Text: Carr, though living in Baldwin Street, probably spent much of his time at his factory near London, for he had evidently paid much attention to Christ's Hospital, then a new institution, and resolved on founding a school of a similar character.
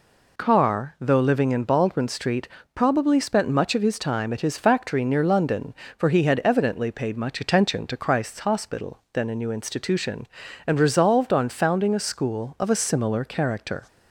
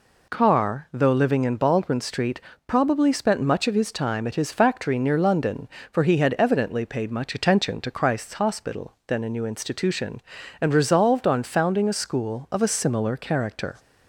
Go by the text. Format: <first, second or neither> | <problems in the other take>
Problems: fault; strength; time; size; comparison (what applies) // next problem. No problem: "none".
neither | none